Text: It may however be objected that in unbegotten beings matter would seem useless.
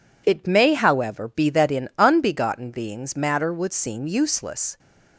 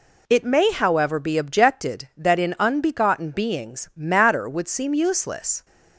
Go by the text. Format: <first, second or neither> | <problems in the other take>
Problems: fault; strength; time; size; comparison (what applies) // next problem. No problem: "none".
second | skips "objected"; at 1.5 s